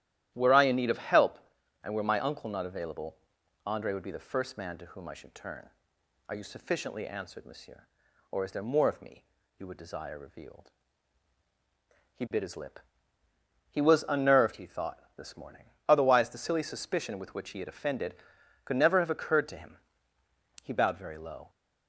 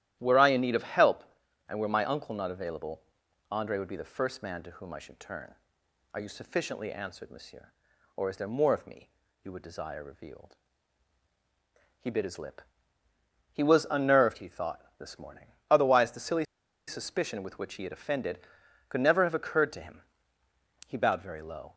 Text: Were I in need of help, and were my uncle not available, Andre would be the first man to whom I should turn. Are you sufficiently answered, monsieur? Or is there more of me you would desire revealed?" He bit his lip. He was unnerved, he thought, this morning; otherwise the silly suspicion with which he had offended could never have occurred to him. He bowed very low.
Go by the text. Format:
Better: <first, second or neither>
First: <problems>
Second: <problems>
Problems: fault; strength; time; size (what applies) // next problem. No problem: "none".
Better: first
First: starts louder than the rest; strong; until 1.3 s; 12.5 dB // pauses between "me" and "you"; slight; at 9.2 s; 0.34 s long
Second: starts louder than the rest; strong; until 1.2 s; 12.5 dB // pauses between "me" and "you"; slight; at 9.0 s; 0.34 s long // pauses between "silly" and "suspicion"; at 16.4 s; 0.42 s long